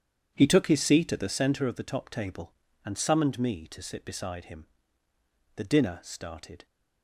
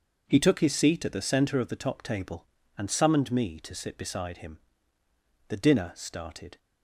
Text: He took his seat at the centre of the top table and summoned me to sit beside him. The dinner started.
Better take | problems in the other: second | starts louder than the rest; strong; until 1.4 s; 8.5 dB

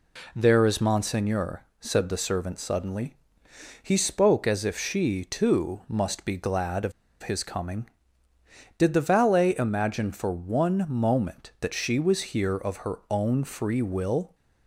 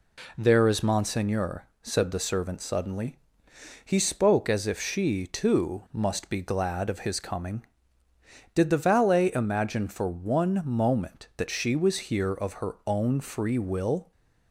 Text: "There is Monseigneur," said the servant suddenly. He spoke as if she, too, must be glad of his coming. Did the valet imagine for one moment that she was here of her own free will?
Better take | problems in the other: second | pauses between "of" and "his"; slight; at 6.9 s; 0.30 s long

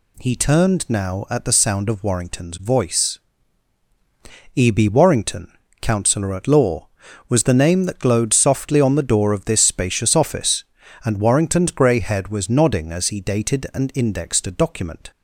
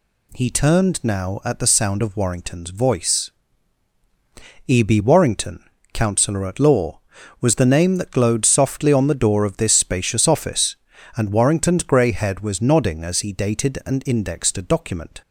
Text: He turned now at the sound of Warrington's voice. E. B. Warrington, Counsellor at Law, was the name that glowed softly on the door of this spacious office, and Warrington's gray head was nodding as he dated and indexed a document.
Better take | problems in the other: neither | none

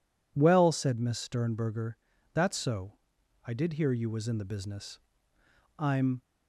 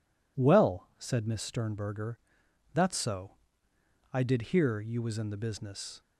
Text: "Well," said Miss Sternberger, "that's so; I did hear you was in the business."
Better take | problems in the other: second | goes on to say "I'm"; slight; from 5.7 s on; 0.46 s long

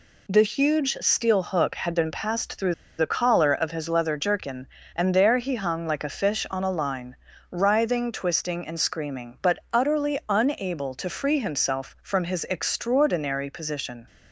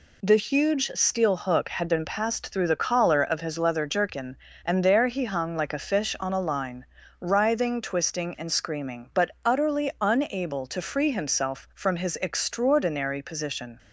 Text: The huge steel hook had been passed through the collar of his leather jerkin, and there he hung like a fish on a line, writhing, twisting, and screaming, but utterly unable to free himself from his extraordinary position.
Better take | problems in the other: second | pauses between "through" and "the"; slight; at 2.7 s; 0.25 s long // pauses between "but" and "utterly"; slight; at 9.5 s; 0.16 s long; slight in the second

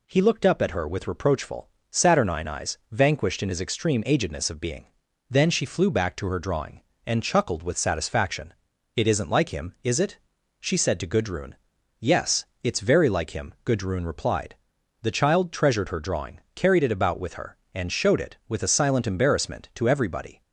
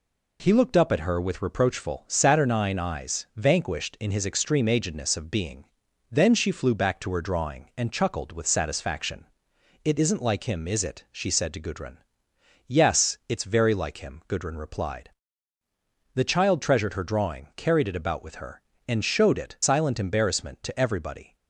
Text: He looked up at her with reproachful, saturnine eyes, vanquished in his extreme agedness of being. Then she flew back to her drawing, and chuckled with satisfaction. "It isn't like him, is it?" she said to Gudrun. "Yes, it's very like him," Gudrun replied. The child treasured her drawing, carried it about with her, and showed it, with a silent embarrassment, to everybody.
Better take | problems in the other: first | skips "with a"; at 19.5 s

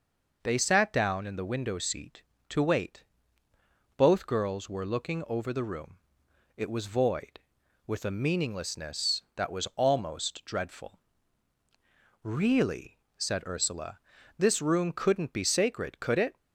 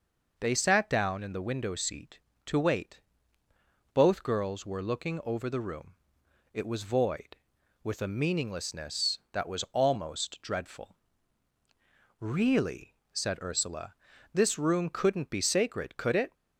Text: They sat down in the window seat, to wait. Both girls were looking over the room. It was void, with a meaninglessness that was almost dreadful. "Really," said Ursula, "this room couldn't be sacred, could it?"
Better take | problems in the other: neither | none

